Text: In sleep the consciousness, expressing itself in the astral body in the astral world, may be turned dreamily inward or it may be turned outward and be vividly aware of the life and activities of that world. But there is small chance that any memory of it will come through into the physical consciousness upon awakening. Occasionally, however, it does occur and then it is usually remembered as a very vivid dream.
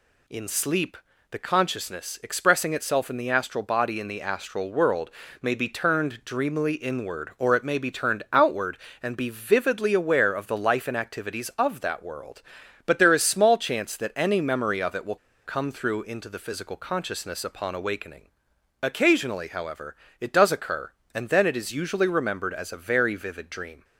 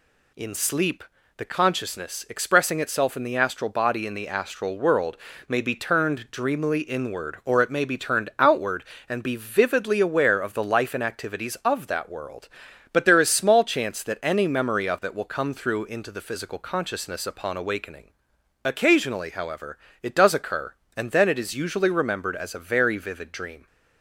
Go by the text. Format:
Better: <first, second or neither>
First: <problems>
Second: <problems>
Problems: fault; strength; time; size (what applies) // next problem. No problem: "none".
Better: second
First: pauses between "sleep" and "the"; slight; at 0.9 s; 0.34 s long // pauses between "will" and "come"; slight; at 15.1 s; 0.28 s long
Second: pauses between "sleep" and "the"; slight; at 1.0 s; 0.34 s long